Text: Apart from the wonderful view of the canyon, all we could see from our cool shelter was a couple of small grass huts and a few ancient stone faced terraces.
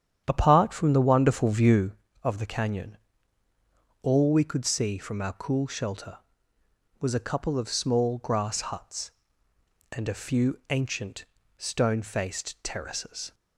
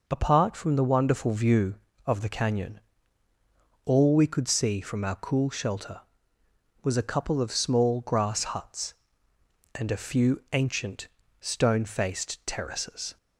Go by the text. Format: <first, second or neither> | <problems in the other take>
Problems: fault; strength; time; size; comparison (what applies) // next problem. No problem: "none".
second | starts louder than the rest; strong; until 2.0 s; 9 dB // pauses between "ancient" and "stone"; slight; at 11.2 s; 0.32 s long; slight in the second